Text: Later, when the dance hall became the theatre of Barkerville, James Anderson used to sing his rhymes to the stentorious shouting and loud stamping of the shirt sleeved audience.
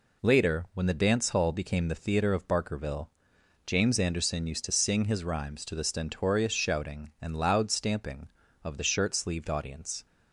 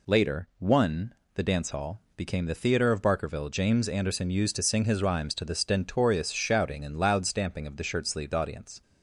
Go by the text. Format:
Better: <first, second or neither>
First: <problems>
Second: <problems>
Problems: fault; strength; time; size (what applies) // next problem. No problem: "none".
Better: first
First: none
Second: says "one" for "when"; at 0.5 s